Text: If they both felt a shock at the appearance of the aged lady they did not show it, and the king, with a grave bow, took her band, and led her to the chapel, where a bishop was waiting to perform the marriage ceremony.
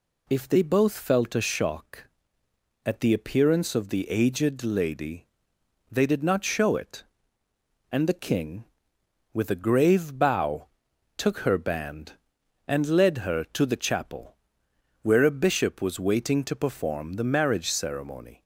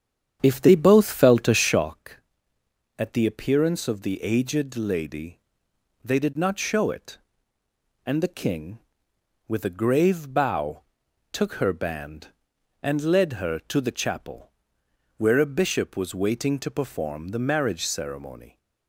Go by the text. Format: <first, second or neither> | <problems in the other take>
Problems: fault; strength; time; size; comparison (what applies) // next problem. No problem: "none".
first | starts louder than the rest; strong; until 2.0 s; 8.5 dB // pauses between "lady" and "they"; noticeable; at 5.3 s; 0.64 s long; noticeable in the first